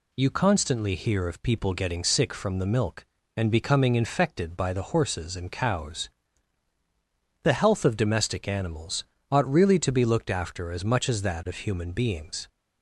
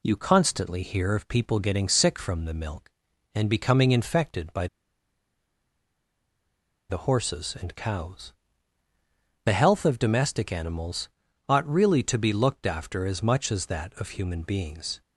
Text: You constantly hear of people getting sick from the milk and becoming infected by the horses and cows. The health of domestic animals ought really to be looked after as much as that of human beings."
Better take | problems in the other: first | pauses between "by" and "the"; strong; at 4.6 s; 2.2 s long // pauses between "animals" and "ought"; at 11.0 s; 0.40 s long; slight in the first

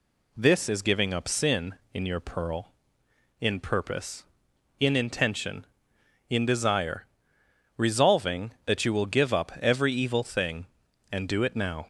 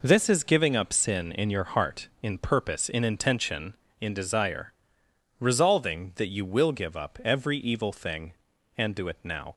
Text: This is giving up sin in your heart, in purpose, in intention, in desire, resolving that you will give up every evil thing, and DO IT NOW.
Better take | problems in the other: second | says "pearl" for "heart"; at 2.1 s

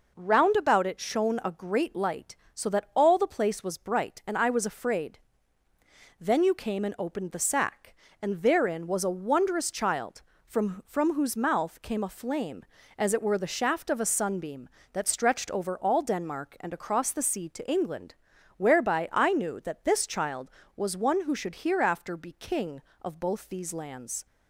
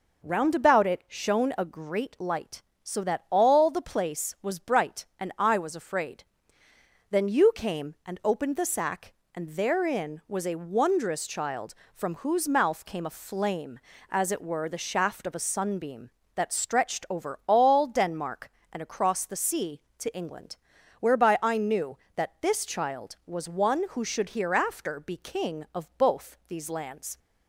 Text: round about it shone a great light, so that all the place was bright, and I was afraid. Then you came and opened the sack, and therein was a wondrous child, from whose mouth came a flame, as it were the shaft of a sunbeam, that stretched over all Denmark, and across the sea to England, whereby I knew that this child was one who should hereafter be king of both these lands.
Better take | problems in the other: second | says "from" twice; at 10.8 s

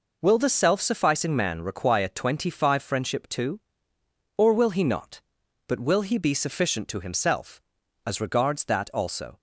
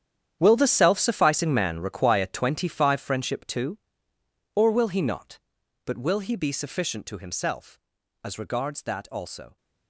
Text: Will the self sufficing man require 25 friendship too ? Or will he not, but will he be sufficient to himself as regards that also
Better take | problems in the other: first | gets quieter; strong; throughout; 15 dB

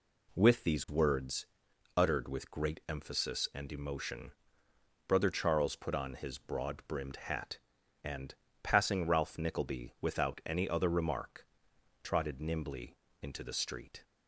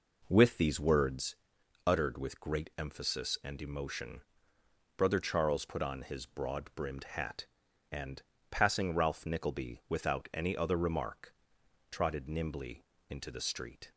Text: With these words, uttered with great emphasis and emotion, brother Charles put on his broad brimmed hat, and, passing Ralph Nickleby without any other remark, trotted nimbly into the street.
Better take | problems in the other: first | starts louder than the rest; noticeable; until 1.3 s; 4.5 dB // pauses between "nimbly" and "into"; slight; at 12.8 s; 0.26 s long; slight in the first

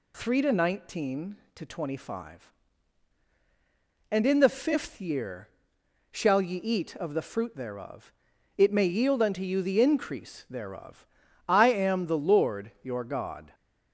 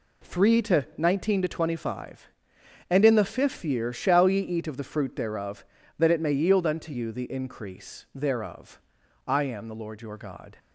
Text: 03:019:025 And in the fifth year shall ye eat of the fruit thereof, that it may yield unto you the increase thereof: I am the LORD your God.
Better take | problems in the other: second | pauses between "year" and "shall"; noticeable; at 5.4 s; 0.60 s long // skips "that"; at 8.3 s

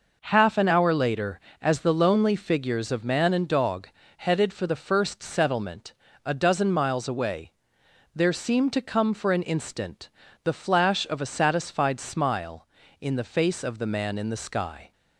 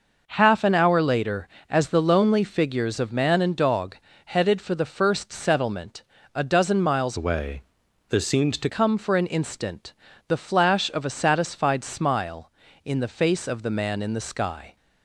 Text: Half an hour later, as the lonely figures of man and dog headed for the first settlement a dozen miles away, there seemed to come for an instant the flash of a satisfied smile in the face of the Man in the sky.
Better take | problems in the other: first | pauses between "dog" and "headed"; slight; at 3.9 s; 0.30 s long; slight in the first // pauses between "settlement" and "a"; slight; at 6.0 s; 0.30 s long; slight in the first // changes voice from "away" to "to"; from 7.1 to 8.6 s; 1.5 s long // pauses between "instant" and "the"; slight; at 9.9 s; 0.34 s long; slight in the first

